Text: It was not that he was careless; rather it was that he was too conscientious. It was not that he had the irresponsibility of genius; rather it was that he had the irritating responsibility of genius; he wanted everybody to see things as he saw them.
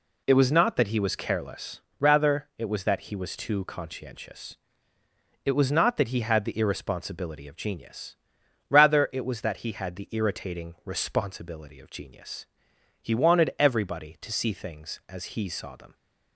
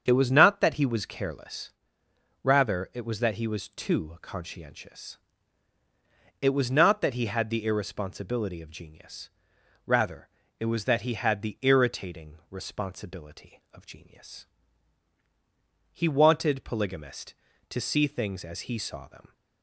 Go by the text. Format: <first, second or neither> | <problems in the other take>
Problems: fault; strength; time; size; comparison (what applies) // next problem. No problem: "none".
first | starts louder than the rest; strong; until 1.0 s; 7 dB // pauses between "rather" and "it"; slight; at 10.2 s; 0.32 s long // says "polygamist" for "everybody"; at 16.6 s